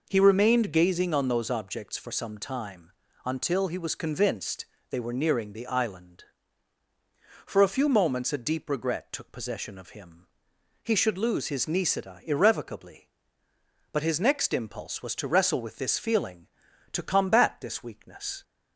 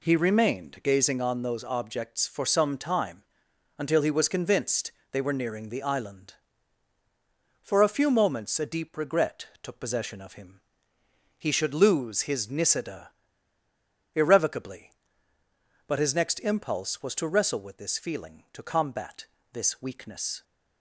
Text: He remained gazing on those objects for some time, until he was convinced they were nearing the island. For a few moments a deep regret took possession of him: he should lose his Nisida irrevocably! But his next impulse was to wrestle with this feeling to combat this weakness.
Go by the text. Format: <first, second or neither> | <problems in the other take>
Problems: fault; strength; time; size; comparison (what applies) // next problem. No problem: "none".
first | pauses between "convinced" and "they"; slight; at 4.9 s; 0.22 s long; slight in the first // pauses between "regret" and "took"; slight; at 9.4 s; 0.16 s long // pauses between "Nisida" and "irrevocably"; at 13.1 s; 1.0 s long // pauses between "combat" and "this"; slight; at 19.2 s; 0.28 s long